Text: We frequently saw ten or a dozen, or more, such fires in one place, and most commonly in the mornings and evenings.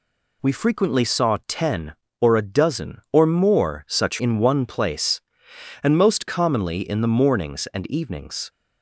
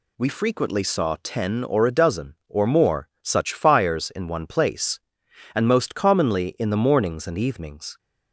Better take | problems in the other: second | skips "fires"; at 4.1 s

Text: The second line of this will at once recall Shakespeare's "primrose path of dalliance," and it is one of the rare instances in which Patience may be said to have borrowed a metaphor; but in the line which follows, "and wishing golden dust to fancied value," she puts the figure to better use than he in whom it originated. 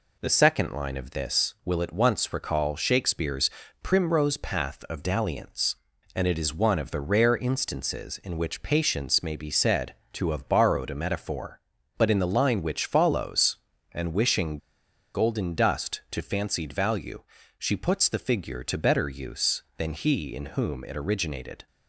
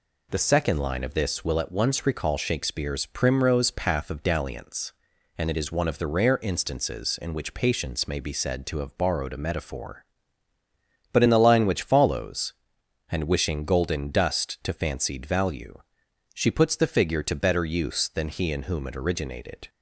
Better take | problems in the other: second | pauses between "Shakespeare's" and "primrose"; slight; at 3.5 s; 0.34 s long // pauses between "wishing" and "golden"; noticeable; at 14.5 s; 0.56 s long

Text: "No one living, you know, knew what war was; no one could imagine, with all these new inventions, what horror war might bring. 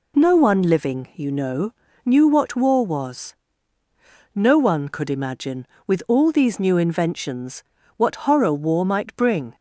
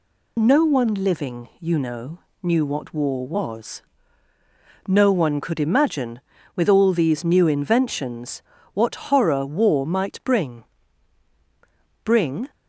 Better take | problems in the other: first | says "bring" twice; at 12.0 s

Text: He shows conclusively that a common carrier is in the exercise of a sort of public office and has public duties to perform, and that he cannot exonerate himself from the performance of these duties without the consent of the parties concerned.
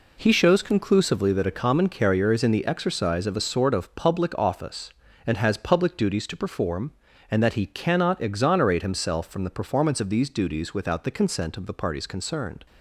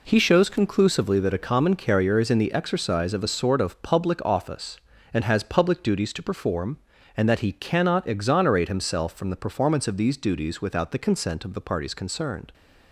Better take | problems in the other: neither | none

